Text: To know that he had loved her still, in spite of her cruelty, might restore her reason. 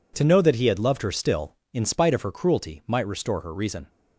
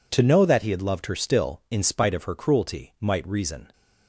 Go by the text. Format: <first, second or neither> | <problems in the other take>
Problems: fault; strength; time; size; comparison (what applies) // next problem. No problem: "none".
first | skips "restore her"; at 3.2 s